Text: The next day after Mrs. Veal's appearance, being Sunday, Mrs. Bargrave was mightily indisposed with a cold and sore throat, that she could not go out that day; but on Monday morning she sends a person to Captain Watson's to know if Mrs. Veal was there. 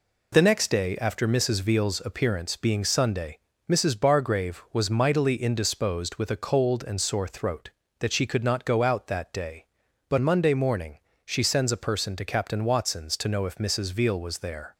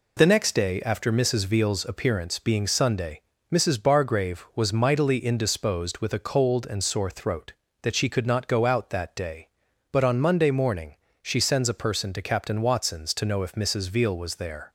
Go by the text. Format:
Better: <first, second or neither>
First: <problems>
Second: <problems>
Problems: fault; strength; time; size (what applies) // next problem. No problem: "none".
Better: second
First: skips "on"; at 10.1 s // pauses between "morning" and "she"; slight; at 10.9 s; 0.28 s long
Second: pauses between "morning" and "she"; slight; at 10.9 s; 0.28 s long